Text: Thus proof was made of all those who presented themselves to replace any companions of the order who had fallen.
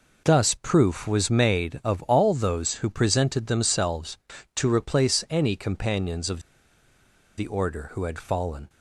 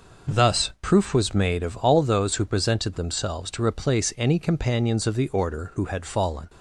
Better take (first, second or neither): second